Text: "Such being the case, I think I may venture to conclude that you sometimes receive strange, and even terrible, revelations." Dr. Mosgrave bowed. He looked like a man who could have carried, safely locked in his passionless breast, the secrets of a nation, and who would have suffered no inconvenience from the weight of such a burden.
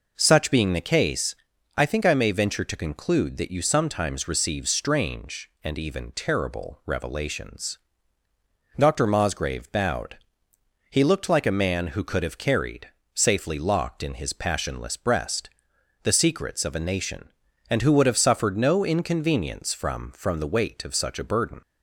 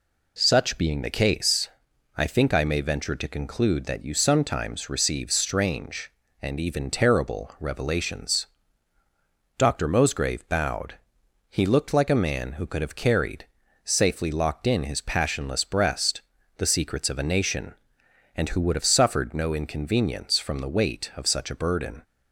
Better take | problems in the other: second | says "from" twice; at 20.1 s

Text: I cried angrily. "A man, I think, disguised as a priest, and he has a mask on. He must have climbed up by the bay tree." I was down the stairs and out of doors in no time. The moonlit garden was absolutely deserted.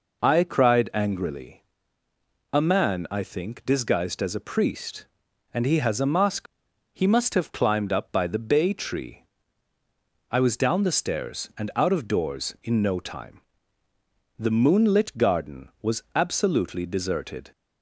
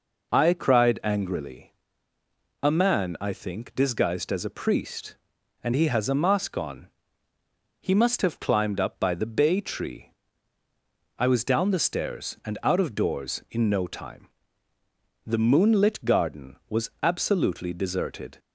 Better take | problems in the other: second | skips "on"; at 6.6 s

